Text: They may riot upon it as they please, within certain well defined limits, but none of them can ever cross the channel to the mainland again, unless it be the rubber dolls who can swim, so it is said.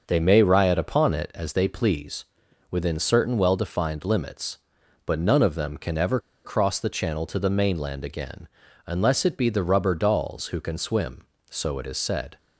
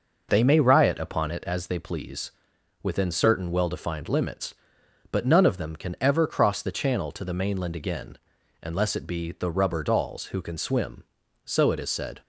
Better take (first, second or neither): second